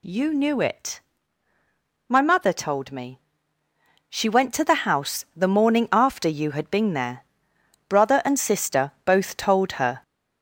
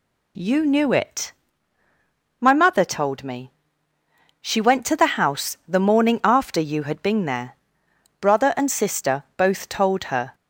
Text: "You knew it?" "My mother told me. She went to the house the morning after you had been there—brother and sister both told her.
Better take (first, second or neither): second